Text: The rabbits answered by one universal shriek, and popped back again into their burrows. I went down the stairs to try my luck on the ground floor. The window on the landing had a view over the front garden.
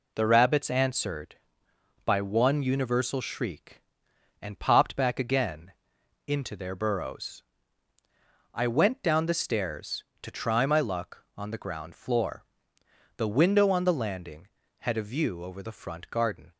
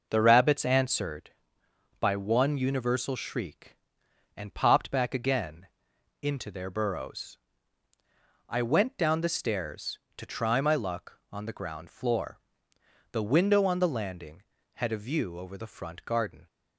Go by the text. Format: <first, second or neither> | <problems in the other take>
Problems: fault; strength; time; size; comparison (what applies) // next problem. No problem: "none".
first | starts louder than the rest; noticeable; until 1.2 s; 5.5 dB // pauses between "again" and "into"; noticeable; at 5.6 s; 0.56 s long; noticeable in the first